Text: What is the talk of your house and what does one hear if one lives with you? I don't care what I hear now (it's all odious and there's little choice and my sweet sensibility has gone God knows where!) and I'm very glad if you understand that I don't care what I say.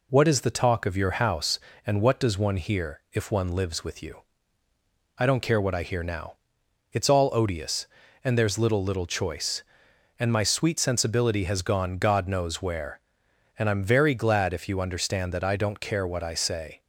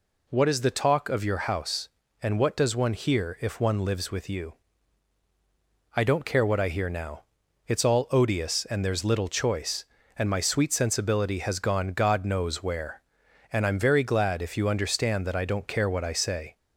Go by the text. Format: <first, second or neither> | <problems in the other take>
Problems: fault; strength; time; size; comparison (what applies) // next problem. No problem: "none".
second | says "little" twice; at 8.8 s